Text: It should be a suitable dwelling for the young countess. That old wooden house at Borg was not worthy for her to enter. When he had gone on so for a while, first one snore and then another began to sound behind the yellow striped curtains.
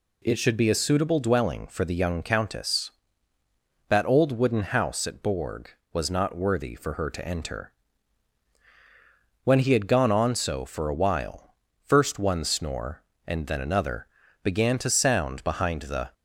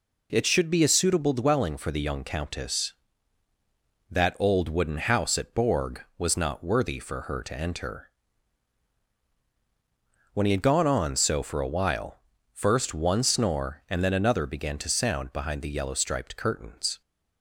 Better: second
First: pauses between "another" and "began"; slight; at 14.0 s; 0.36 s long // stops before "yellow striped curtains"; at 16.1 s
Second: none

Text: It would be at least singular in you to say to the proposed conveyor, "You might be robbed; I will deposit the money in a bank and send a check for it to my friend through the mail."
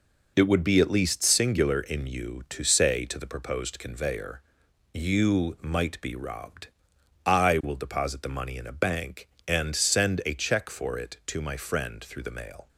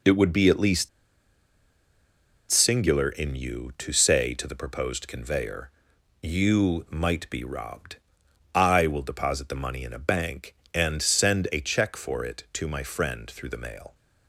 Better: first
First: none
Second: pauses between "least" and "singular"; strong; at 0.8 s; 1.6 s long

